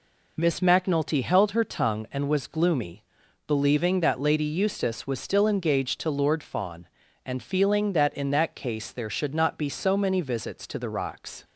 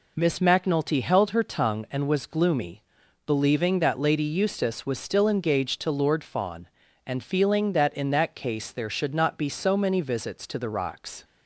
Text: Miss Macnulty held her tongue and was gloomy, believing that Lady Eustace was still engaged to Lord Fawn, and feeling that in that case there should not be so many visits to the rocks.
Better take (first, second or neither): neither